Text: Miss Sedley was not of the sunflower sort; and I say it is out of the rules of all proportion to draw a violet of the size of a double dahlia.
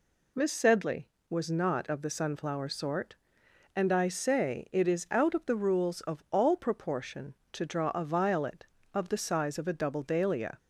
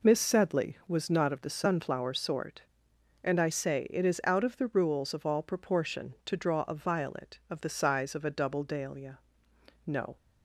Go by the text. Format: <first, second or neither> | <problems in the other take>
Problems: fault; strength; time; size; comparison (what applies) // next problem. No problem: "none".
first | goes on to say "No"; slight; from 9.8 s on; 0.30 s long